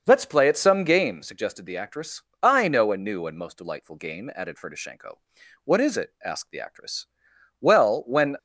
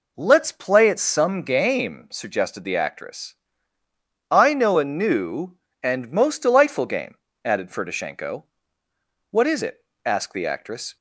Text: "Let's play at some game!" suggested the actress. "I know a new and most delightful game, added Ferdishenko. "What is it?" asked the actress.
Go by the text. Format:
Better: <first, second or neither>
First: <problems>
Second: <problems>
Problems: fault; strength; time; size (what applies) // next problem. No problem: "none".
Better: second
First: starts louder than the rest; until 1.0 s; 6 dB // goes on to say "Well when"; noticeable; from 7.6 s on; 0.74 s long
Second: none